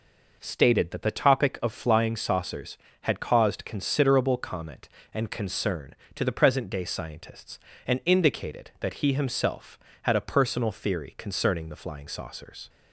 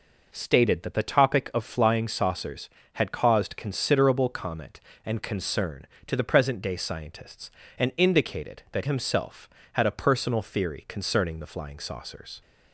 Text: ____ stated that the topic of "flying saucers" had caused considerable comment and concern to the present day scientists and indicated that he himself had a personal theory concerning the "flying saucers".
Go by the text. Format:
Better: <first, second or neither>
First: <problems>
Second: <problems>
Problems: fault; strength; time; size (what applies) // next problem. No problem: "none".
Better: first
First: none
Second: skips "he"; at 8.8 s